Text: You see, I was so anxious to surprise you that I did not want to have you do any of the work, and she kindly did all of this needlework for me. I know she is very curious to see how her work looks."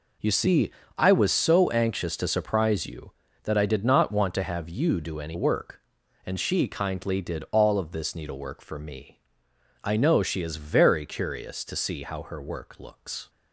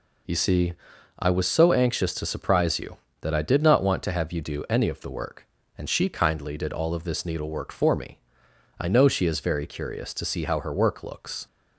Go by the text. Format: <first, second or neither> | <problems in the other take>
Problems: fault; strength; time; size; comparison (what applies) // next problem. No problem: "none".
second | skips "of the"; at 5.3 s